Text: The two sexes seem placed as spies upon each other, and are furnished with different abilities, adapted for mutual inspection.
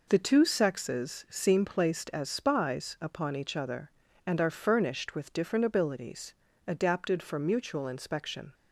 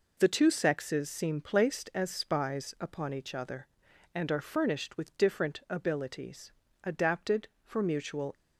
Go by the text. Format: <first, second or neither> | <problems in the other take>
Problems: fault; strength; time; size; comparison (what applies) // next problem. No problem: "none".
first | stops before "inspection"; at 8.3 s